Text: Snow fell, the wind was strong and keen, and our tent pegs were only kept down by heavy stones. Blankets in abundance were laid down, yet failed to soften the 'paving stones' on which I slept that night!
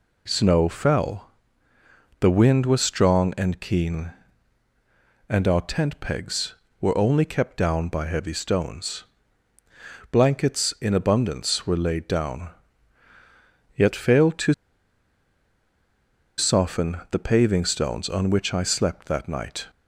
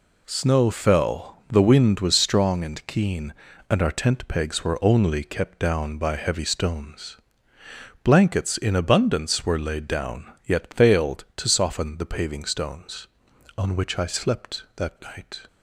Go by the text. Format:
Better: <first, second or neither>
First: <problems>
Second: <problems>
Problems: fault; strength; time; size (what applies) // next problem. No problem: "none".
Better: second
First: pauses between "to" and "soften"; strong; at 14.5 s; 1.8 s long // pauses between "soften" and "the"; slight; at 16.9 s; 0.16 s long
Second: none